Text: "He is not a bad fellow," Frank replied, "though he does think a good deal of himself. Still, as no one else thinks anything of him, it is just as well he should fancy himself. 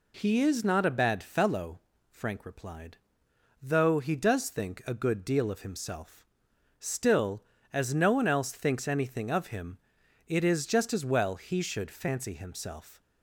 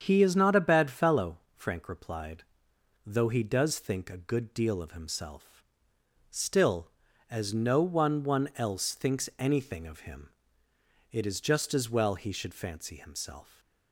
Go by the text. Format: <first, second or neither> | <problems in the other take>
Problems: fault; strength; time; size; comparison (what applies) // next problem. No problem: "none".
first | starts louder than the rest; strong; until 1.0 s; 7.5 dB // says "one" twice; at 8.2 s